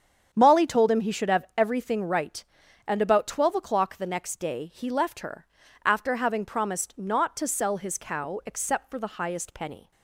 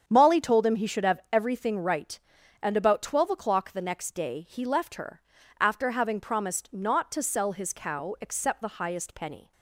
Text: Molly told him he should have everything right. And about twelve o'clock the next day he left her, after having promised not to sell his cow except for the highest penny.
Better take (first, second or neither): first